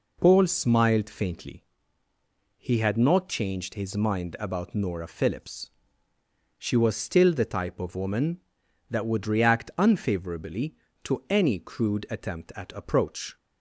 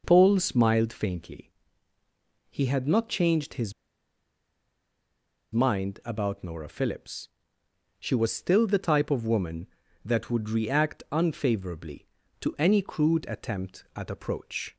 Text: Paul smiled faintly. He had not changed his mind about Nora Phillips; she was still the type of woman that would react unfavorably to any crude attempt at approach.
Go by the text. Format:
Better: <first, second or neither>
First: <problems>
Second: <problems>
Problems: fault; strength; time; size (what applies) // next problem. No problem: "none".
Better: first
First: none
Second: pauses between "his" and "mind"; strong; at 3.7 s; 1.7 s long